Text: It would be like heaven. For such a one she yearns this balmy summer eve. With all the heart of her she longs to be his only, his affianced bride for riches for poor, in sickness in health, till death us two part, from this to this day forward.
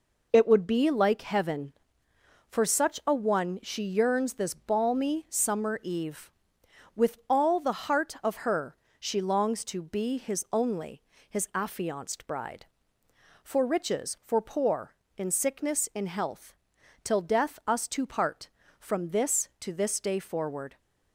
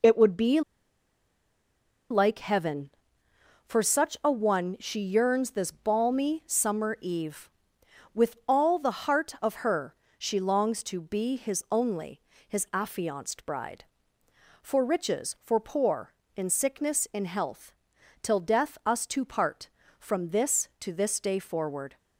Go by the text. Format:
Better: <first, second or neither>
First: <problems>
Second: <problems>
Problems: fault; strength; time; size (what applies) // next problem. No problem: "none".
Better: first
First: pauses between "her" and "she"; slight; at 8.7 s; 0.24 s long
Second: pauses between "be" and "like"; strong; at 0.6 s; 1.5 s long // pauses between "her" and "she"; slight; at 9.9 s; 0.24 s long